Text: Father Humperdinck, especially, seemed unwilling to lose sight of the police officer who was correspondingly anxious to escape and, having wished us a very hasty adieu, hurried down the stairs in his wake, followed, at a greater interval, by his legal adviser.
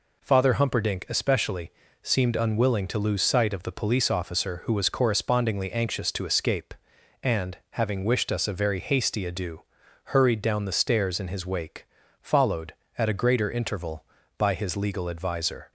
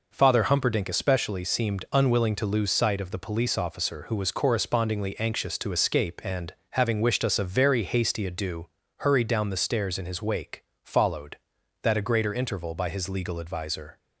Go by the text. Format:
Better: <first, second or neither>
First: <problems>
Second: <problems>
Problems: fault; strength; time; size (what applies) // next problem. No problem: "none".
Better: first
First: none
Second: says "that" for "at"; at 11.8 s